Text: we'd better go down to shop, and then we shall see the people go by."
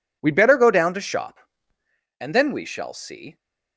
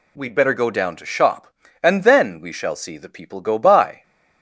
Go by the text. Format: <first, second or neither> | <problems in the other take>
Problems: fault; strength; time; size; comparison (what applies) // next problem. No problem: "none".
second | stops before "the people go by"; at 3.3 s